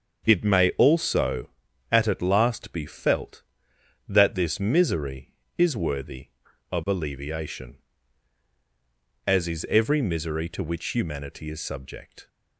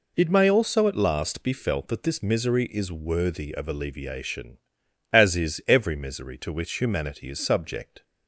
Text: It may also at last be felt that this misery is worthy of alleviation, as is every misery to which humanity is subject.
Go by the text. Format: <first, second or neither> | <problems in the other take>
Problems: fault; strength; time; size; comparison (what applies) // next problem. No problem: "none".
second | starts louder than the rest; until 1.2 s; 6.5 dB // says "at" twice; at 2.0 s